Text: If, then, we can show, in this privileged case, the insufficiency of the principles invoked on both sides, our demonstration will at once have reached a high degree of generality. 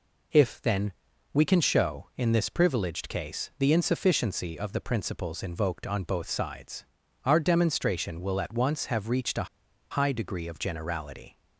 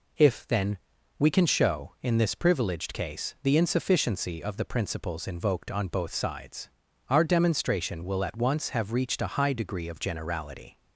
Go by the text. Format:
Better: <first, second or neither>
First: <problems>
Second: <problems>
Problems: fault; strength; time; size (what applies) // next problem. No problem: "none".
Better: second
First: pauses between "a" and "high"; at 9.4 s; 0.45 s long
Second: none